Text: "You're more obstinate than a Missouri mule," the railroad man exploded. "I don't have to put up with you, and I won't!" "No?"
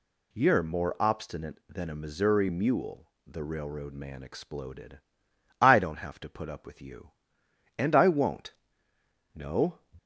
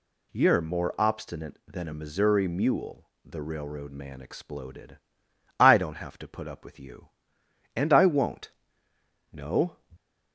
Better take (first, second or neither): neither